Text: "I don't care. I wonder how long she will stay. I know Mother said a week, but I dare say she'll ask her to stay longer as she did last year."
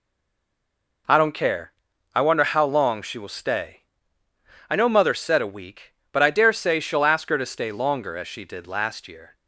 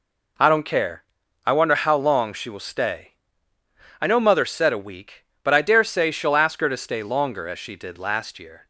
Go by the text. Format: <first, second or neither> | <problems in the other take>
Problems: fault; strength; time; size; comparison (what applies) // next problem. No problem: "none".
second | stays silent before the first word; until 1.0 s; 1.0 s long